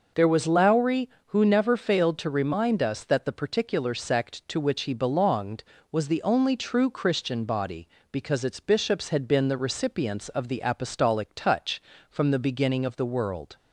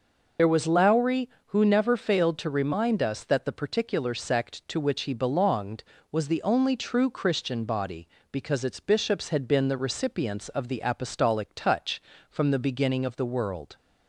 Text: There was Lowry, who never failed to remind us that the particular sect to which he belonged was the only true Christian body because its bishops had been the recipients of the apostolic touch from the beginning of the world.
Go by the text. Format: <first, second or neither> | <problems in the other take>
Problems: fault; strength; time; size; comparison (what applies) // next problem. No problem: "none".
first | loses the start of "There"; at 0.3 s; 40 ms